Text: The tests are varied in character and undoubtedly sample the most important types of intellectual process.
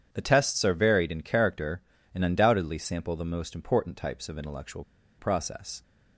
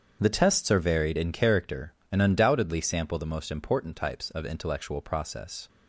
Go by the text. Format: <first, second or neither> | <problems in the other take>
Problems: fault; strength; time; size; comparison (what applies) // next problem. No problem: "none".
second | starts louder than the rest; strong; until 1.1 s; 8.5 dB; strong in the second // pauses between "intellectual" and "process"; slight; at 4.8 s; 0.35 s long